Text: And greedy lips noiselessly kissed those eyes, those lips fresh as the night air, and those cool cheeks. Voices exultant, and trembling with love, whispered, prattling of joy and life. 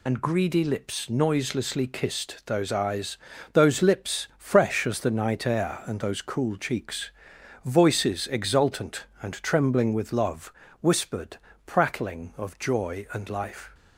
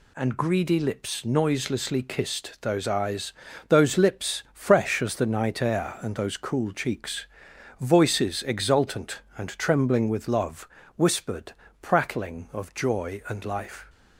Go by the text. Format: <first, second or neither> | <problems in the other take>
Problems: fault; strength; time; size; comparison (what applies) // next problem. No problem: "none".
second | loses the start of "And"; at 0.0 s; 55 ms